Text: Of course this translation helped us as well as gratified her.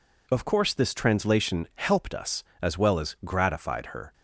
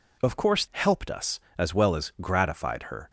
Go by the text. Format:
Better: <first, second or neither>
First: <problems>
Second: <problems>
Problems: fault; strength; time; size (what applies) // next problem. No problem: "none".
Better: first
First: none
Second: skips "this translation"; at 0.6 s